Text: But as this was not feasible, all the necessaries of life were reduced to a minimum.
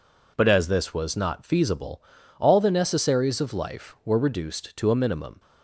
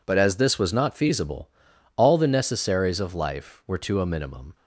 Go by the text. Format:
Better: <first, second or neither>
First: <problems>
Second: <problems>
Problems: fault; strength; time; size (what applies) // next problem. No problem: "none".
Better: first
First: none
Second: skips "reduced"; at 3.7 s